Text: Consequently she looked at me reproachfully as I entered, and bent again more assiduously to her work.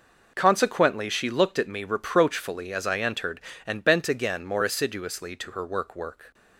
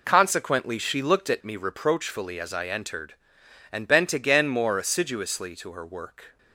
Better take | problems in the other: second | says "work" twice; at 5.9 s

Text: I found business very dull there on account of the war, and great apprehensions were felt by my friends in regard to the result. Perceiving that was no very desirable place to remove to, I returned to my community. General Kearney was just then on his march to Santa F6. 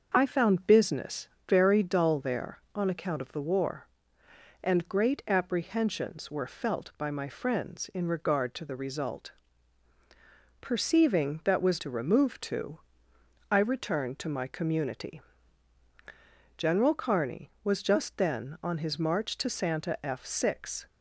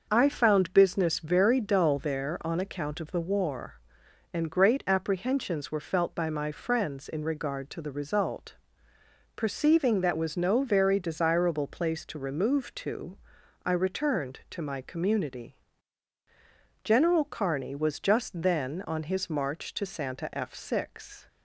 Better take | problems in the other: second | starts louder than the rest; until 1.1 s; 6.5 dB; also in the second // pauses between "business" and "very"; slight; at 1.2 s; 0.22 s long // skips "no very desirable place"; at 11.7 s

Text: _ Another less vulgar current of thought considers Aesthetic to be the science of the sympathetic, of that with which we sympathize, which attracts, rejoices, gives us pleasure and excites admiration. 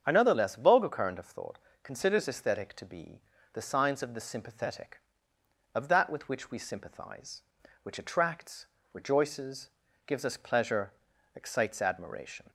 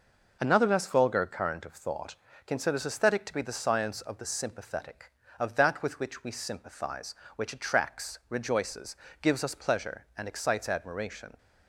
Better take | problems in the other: second | starts louder than the rest; strong; until 1.0 s; 8 dB // pauses between "thought" and "considers"; slight; at 1.5 s; 0.26 s long; slight in the second // pauses between "be" and "the"; slight; at 3.1 s; 0.34 s long // skips "and"; at 11.1 s

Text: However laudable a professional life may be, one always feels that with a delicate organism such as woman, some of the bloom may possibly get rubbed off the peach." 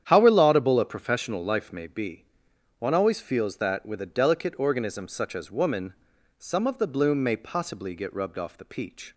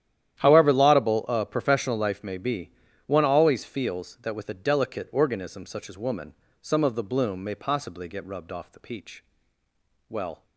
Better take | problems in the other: first | starts louder than the rest; strong; until 1.4 s; 11 dB; strong in the first // goes on to say "Well"; slight; from 10.0 s on; 0.36 s long

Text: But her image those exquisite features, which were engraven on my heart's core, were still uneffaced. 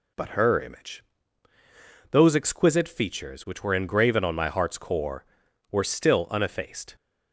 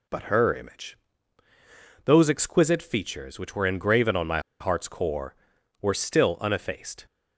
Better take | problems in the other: first | pauses between "image" and "those"; at 0.9 s; 1.0 s long; also in the first // pauses between "my" and "heart's"; slight; at 4.3 s; 0.21 s long

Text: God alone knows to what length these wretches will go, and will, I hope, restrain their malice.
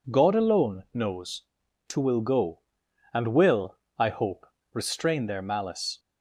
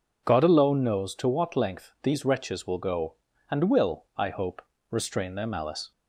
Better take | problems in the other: second | skips "what length these wretches"; at 1.9 s

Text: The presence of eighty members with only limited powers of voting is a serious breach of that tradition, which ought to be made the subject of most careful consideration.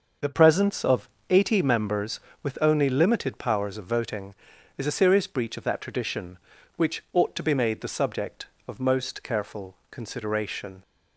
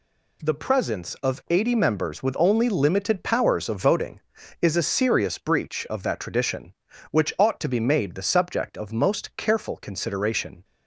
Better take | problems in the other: second | starts louder than the rest; until 1.4 s; 6 dB // changes voice at "presence"; from 0.3 s on; 10.5 s long // pauses between "of" and "eighty"; slight; at 1.0 s; 0.22 s long

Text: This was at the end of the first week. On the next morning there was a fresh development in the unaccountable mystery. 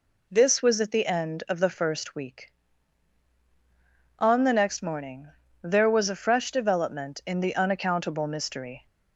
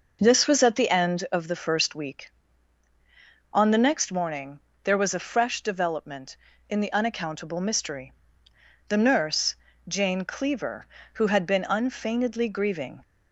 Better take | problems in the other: first | pauses between "morning" and "there"; slight; at 4.5 s; 0.24 s long; slight in the first // goes on to say "The nurse Jane Cleaver who had been unfeignedly grieving"; strong; from 8.8 s on; 4.1 s long

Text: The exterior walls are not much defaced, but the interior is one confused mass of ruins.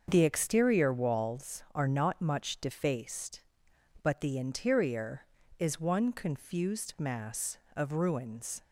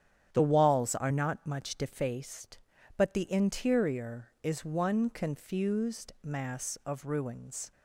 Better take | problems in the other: first | starts louder than the rest; strong; until 1.3 s; 9 dB; also in the first // skips "exterior"; at 0.4 s

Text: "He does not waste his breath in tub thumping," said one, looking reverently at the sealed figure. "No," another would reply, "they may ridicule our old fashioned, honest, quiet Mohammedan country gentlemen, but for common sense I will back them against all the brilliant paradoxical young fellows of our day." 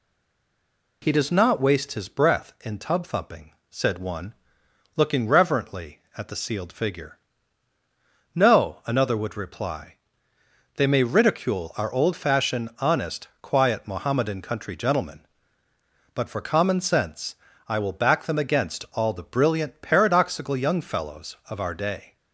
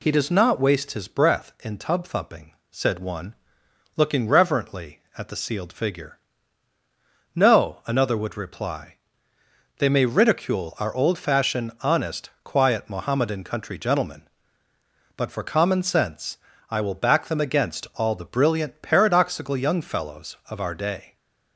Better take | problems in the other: second | stays silent before the first word; until 1.0 s; 1.0 s long // pauses between "sense" and "I"; slight; at 17.3 s; 0.30 s long; slight in the second

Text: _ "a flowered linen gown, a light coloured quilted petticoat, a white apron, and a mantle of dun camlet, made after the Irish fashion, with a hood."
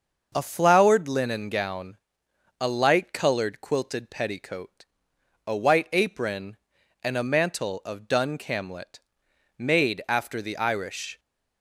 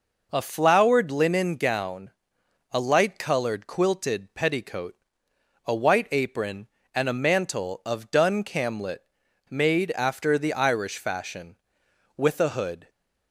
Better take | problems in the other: second | starts louder than the rest; noticeable; until 1.3 s; 6 dB // stops before "fashion with a hood"; at 11.1 s

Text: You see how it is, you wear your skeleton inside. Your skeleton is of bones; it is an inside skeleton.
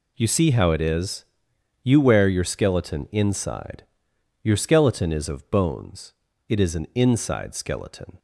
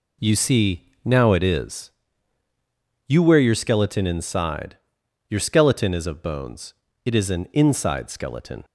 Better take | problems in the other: first | says "now" for "how"; at 1.0 s

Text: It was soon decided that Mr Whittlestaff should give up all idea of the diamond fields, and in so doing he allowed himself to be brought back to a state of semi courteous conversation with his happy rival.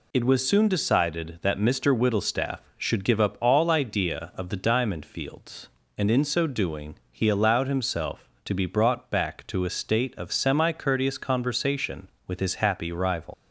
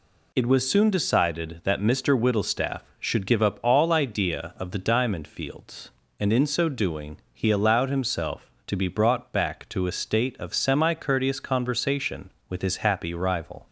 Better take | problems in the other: second | pauses between "doing" and "he"; slight; at 6.9 s; 0.16 s long; slight in the second // leaves "rival" unfinished; at 13.3 s; 105 ms

